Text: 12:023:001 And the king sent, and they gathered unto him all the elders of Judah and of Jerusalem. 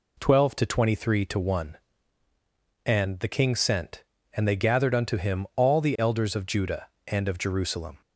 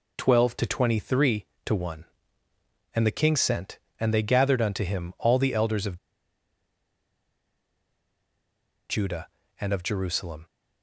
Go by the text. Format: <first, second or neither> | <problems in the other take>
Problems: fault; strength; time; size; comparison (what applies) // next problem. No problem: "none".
first | pauses between "of" and "Judah"; strong; at 5.9 s; 2.9 s long